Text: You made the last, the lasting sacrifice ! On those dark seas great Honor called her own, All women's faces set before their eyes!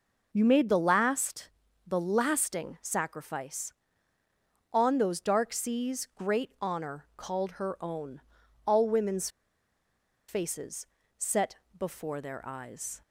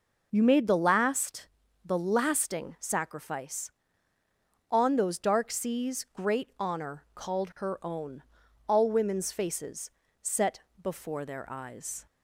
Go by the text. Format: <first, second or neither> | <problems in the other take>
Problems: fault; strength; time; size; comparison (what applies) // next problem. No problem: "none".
second | pauses between "women's" and "faces"; at 9.2 s; 1.0 s long // pauses between "faces" and "set"; slight; at 10.8 s; 0.32 s long; slight in the second // pauses between "set" and "before"; slight; at 11.5 s; 0.24 s long; slight in the second